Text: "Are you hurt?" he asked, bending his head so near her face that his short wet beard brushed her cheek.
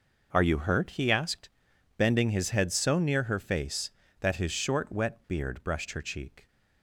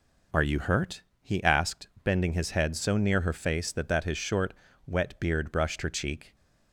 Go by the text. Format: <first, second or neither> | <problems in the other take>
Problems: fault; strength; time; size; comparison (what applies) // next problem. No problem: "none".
first | says "that" twice; at 3.8 s // pauses between "short" and "wet"; slight; at 4.5 s; 0.34 s long